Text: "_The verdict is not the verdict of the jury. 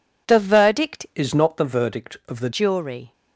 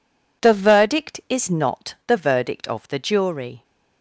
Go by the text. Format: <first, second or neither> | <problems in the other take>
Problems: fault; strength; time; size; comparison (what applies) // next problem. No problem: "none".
second | changes voice from "is" to "the"; from 1.1 to 2.4 s; 1.3 s long